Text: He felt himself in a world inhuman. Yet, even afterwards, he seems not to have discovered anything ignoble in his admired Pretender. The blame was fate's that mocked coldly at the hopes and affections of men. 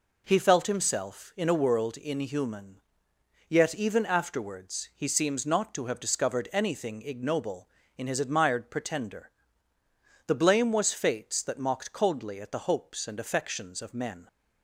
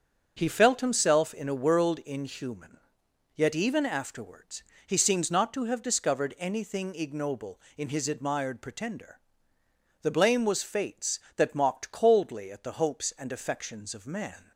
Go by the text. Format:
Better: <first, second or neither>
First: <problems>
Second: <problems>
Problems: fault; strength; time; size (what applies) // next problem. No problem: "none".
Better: first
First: none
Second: starts louder than the rest; until 1.3 s; 6.5 dB // says "man" for "men"; at 14.0 s